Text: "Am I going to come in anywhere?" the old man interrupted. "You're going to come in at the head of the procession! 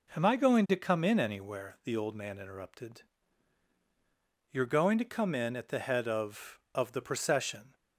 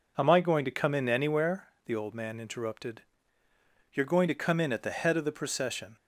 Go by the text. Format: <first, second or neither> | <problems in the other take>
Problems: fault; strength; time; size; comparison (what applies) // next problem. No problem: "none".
second | says "of" twice; at 6.7 s